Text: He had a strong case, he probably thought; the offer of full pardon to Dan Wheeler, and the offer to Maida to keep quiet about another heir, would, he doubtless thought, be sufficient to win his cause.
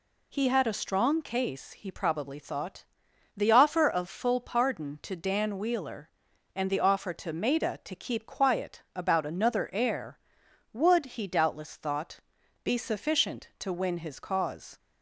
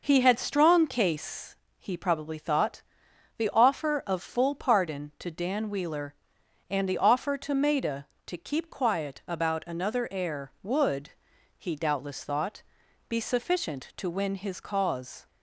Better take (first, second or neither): first